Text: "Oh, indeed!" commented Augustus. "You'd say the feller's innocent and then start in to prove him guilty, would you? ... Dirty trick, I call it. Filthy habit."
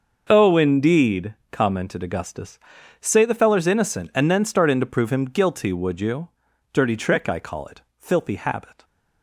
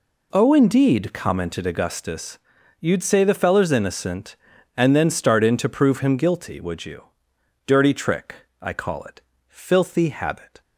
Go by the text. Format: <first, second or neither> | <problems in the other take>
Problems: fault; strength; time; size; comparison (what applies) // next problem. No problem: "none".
second | starts louder than the rest; noticeable; until 1.3 s; 6 dB // skips "You'd"; at 2.7 s